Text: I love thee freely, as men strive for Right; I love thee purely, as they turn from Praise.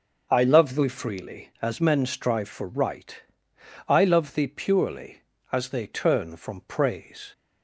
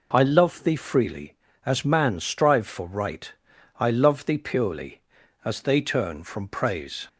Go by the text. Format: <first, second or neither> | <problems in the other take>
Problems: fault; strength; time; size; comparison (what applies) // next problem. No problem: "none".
first | says "man" for "men"; at 1.8 s